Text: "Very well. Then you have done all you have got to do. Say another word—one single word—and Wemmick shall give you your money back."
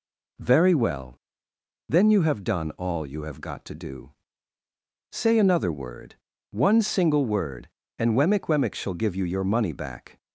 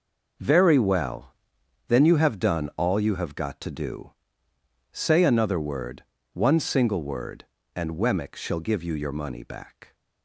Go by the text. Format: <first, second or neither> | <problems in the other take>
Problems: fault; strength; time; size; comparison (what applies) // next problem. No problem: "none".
second | says "Wemmick" twice; at 8.4 s